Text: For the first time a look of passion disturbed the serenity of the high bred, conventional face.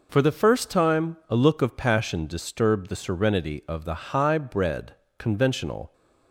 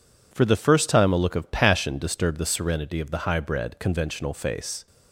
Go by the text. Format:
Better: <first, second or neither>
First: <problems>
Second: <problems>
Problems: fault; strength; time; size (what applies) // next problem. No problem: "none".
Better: second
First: stops before "face"; at 5.9 s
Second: none